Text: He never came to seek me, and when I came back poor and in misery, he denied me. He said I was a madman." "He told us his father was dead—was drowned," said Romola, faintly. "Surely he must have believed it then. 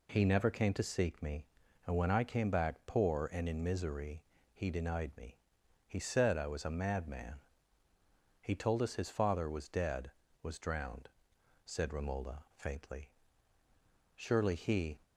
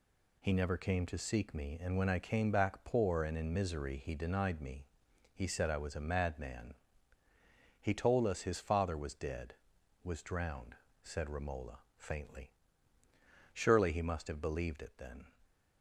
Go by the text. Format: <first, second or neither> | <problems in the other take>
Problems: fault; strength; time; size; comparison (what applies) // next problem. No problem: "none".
second | stops before "must have believed it then"; at 15.0 s